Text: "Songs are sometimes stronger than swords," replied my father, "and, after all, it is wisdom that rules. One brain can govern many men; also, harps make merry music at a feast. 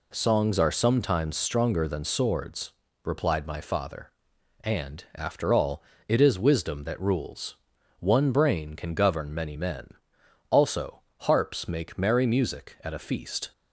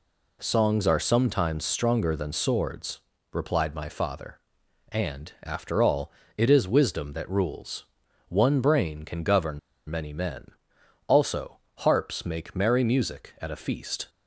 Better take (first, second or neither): first